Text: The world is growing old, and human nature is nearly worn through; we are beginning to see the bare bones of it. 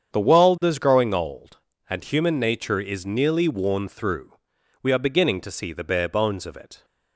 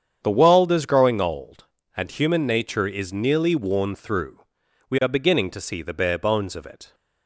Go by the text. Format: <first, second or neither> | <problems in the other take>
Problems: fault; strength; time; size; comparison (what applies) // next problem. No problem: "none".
neither | starts louder than the rest; strong; the same in both